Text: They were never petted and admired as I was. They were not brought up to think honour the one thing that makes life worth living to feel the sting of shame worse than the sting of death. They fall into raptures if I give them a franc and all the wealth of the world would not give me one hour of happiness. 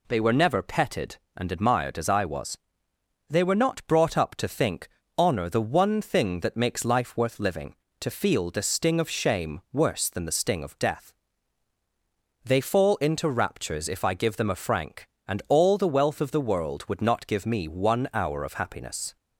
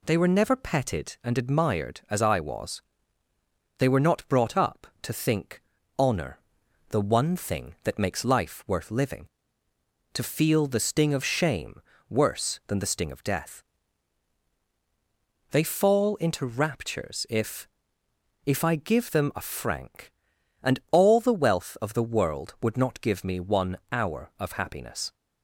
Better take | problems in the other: first | pauses between "think" and "honour"; slight; at 5.6 s; 0.36 s long; slight in the first // pauses between "honour" and "the"; noticeable; at 6.3 s; 0.50 s long // pauses between "shame" and "worse"; slight; at 11.7 s; 0.30 s long // says "if" twice; at 18.4 s

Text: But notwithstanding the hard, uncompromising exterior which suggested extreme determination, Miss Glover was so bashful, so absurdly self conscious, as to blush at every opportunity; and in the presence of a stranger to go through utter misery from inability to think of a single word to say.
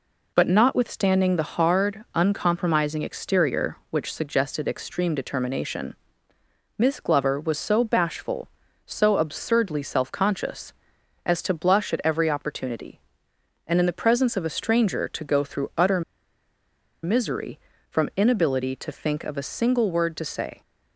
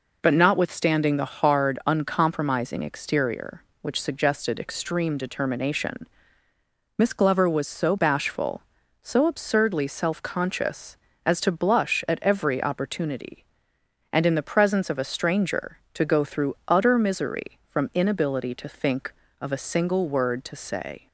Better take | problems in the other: second | pauses between "utter" and "misery"; at 16.0 s; 1.0 s long

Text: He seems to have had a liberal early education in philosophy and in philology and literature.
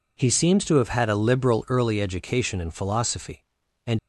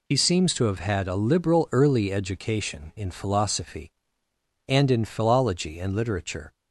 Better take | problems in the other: second | stops before "in philology and literature"; at 3.9 s

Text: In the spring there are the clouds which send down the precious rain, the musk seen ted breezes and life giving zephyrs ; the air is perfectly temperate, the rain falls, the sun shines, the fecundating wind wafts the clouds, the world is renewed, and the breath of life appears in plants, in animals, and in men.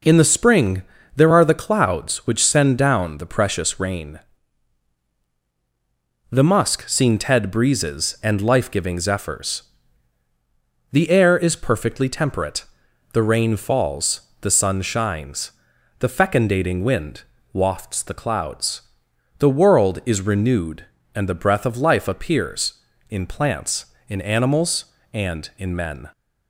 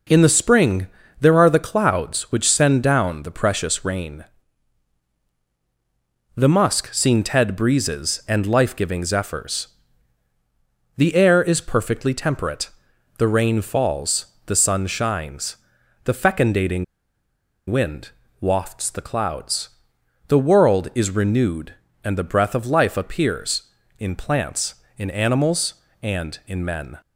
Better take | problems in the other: first | pauses between "spring" and "there"; slight; at 0.8 s; 0.32 s long; slight in the first // pauses between "fecundating" and "wind"; noticeable; at 16.8 s; 0.85 s long // pauses between "wind" and "wafts"; slight; at 18.1 s; 0.30 s long; slight in the first

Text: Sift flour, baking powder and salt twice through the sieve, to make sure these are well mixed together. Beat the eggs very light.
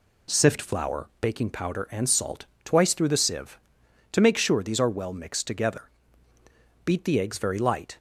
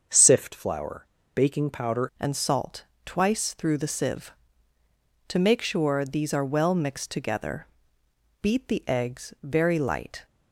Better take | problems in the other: first | starts louder than the rest; until 1.4 s; 6.5 dB // changes voice at "and"; from 2.1 s on; 8.1 s long // pauses between "salt" and "twice"; slight; at 2.8 s; 0.20 s long; slight in the first

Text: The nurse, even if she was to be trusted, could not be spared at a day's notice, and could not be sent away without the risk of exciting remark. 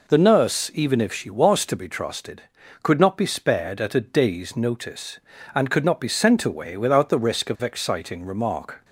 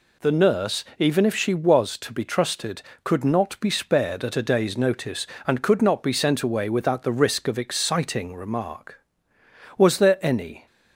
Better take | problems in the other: first | goes on to say "Was there any"; noticeable; from 9.7 s on; 0.90 s long

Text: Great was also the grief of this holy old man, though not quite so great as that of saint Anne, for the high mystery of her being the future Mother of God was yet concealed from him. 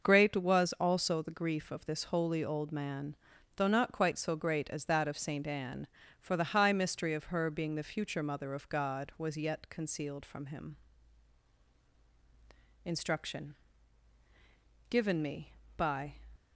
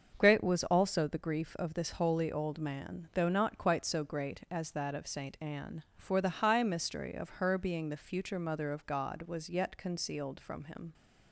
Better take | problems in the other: second | starts louder than the rest; noticeable; until 1.1 s; 6 dB; also in the second // goes on to say "INSTRUCTION GIVEN ME BY"; strong; from 12.8 s on; 3.3 s long

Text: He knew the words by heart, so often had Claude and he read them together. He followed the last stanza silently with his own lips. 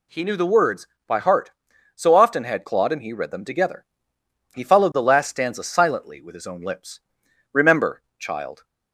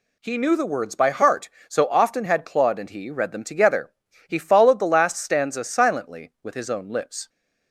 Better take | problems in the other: second | goes on to say "Remember child"; noticeable; from 7.5 s on; 1.1 s long

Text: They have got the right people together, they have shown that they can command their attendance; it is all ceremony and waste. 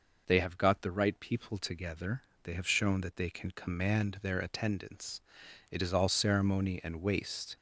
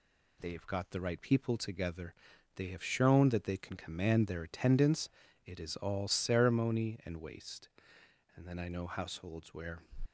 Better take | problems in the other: first | goes on to say "And then I know households where"; from 8.3 s on; 1.4 s long

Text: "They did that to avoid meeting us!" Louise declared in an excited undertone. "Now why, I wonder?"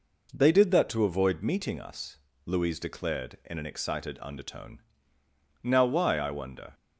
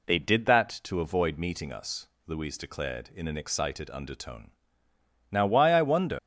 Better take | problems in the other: first | leaves "wonder" unfinished; at 6.1 s; 95 ms

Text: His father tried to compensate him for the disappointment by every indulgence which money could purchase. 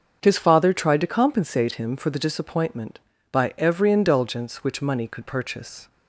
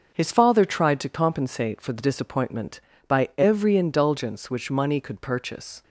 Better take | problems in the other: first | starts louder than the rest; until 1.1 s; 6 dB; also in the first // skips "him"; at 1.8 s

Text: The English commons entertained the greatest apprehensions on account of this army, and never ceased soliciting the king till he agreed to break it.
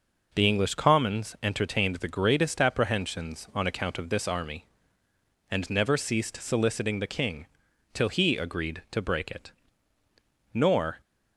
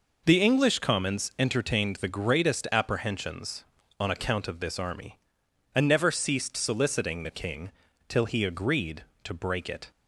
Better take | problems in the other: second | pauses between "king" and "till"; noticeable; at 7.4 s; 0.46 s long; slight in the second // goes on to say "Nor"; slight; from 10.5 s on; 0.46 s long

